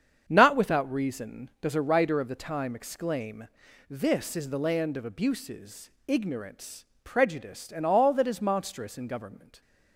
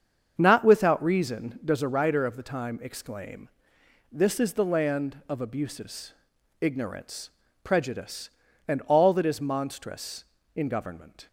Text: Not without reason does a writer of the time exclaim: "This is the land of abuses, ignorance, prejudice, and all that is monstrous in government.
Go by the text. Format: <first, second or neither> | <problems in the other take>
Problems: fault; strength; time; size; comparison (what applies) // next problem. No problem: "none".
neither | starts louder than the rest; strong; the same in both